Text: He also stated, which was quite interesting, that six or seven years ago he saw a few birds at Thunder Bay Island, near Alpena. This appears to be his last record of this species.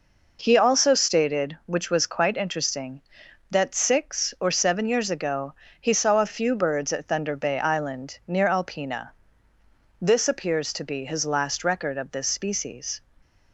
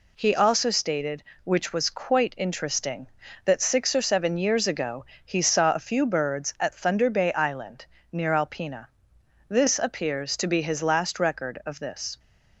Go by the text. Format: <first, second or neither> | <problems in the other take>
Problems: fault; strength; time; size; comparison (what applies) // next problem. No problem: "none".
first | pauses between "ago" and "he"; slight; at 5.0 s; 0.20 s long; slight in the first // stops before "species"; at 12.1 s